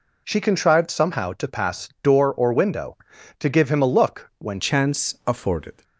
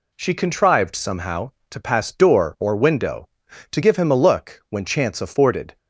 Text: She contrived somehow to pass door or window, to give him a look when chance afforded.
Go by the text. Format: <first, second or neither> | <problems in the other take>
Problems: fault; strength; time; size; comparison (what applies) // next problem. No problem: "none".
second | changes voice at "chance"; from 4.5 s on; 1.3 s long